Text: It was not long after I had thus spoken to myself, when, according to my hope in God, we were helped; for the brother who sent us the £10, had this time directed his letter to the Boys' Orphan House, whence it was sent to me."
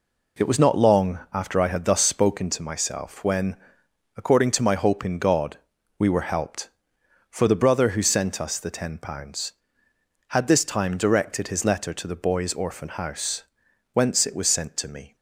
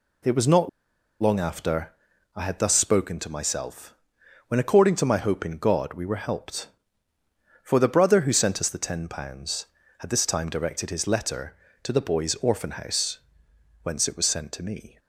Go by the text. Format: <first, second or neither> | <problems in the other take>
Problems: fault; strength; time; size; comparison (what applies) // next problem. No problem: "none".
first | pauses between "not" and "long"; noticeable; at 0.6 s; 0.52 s long // pauses between "after" and "I"; at 1.9 s; 0.42 s long